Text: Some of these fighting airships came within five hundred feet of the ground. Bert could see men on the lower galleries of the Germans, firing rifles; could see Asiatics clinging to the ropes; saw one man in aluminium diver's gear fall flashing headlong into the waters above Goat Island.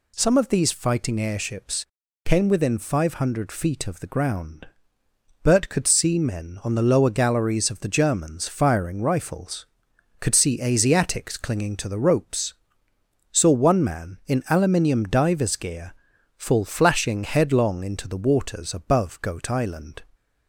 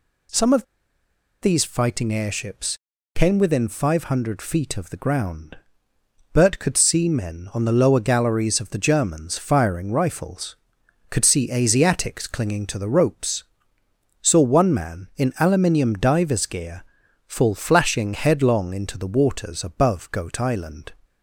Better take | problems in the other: first | pauses between "of" and "these"; noticeable; at 0.6 s; 0.79 s long // pauses between "airships" and "came"; at 2.7 s; 0.40 s long; also in the first // pauses between "gear" and "fall"; at 16.8 s; 0.42 s long; also in the first

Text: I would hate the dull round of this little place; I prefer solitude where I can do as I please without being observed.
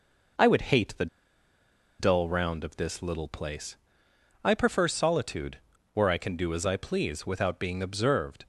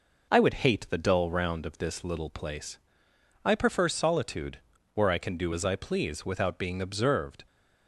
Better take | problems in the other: second | pauses between "the" and "dull"; noticeable; at 1.0 s; 0.93 s long // pauses between "solitude" and "where"; slight; at 5.5 s; 0.34 s long; slight in the second

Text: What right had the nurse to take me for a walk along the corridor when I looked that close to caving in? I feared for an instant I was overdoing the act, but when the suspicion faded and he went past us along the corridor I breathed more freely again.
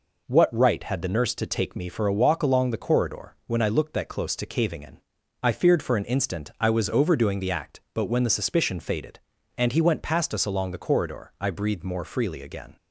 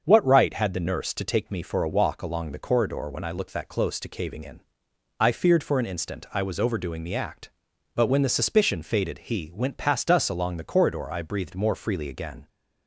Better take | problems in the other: first | starts louder than the rest; until 1.0 s; 6.5 dB // skips "and"; at 9.1 s

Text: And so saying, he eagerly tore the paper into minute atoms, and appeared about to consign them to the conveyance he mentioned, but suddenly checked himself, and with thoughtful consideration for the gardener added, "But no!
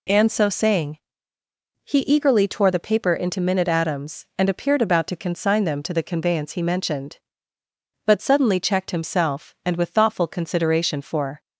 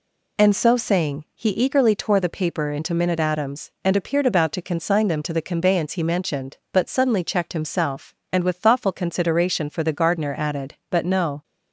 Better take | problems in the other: second | stops before "the gardener added But no"; at 11.3 s

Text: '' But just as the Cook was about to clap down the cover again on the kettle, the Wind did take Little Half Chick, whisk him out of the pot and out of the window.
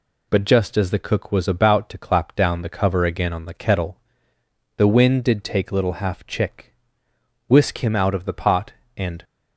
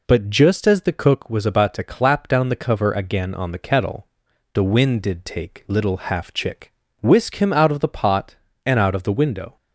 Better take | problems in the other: second | stops before "out of the window"; at 9.2 s

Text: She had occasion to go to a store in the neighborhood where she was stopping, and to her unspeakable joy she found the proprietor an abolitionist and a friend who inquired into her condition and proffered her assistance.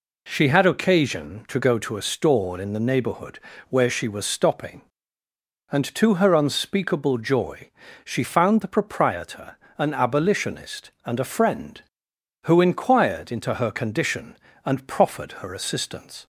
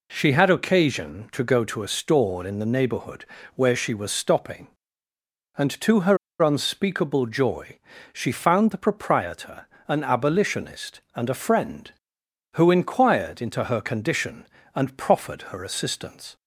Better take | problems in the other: first | pauses between "neighborhood" and "where"; slight; at 3.2 s; 0.30 s long; slight in the first // pauses between "her" and "unspeakable"; slight; at 6.1 s; 0.24 s long // pauses between "joy" and "she"; slight; at 7.7 s; 0.34 s long; slight in the first // pauses between "proprietor" and "an"; slight; at 9.6 s; 0.20 s long; slight in the first

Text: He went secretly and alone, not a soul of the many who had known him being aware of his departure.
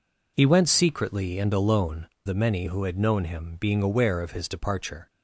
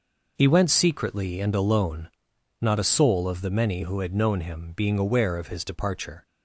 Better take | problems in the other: second | skips "not a soul of"; at 2.1 s

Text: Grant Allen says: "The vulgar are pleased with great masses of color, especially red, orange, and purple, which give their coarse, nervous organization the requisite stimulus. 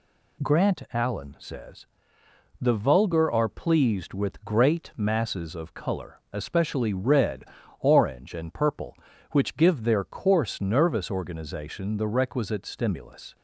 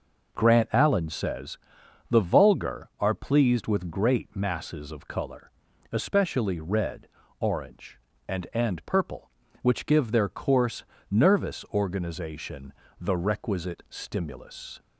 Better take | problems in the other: first | says "and" twice; at 8.5 s // pauses between "organization" and "the"; slight; at 12.7 s; 0.26 s long

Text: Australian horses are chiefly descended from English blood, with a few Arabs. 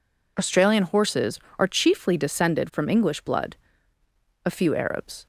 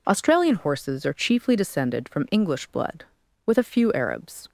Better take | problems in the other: second | skips "with"; at 4.0 s

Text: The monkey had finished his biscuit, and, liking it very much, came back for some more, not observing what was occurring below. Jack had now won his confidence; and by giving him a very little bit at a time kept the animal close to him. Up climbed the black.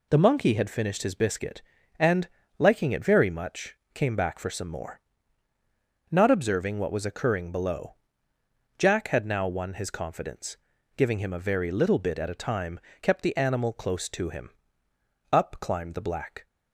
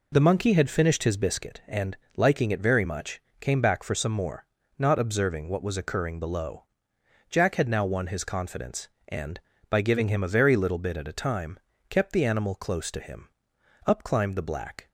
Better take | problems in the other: second | skips "and by"; at 10.7 s // pauses between "time" and "kept"; slight; at 12.8 s; 0.20 s long; slight in the second

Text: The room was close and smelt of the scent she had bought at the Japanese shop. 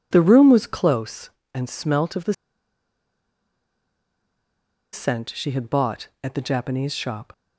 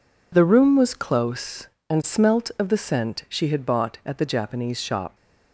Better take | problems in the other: second | pauses between "the" and "scent"; strong; at 2.3 s; 2.5 s long

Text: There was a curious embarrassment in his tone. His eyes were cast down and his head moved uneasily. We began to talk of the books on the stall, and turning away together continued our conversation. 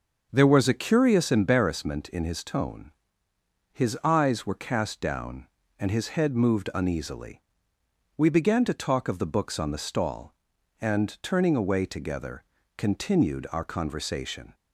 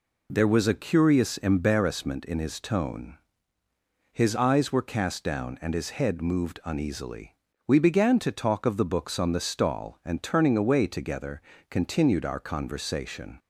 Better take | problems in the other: second | starts louder than the rest; until 1.6 s; 6.5 dB // pauses between "together" and "continued"; slight; at 12.4 s; 0.34 s long; slight in the second

